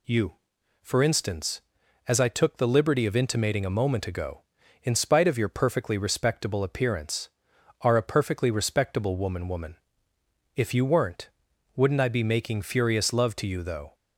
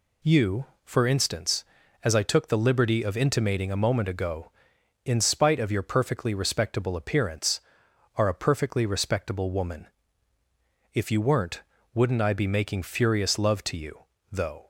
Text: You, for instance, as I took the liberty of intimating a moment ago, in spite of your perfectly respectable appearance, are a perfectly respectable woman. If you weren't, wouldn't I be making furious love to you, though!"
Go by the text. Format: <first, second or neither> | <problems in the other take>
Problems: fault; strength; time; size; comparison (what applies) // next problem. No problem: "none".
second | says "woman" twice; at 9.4 s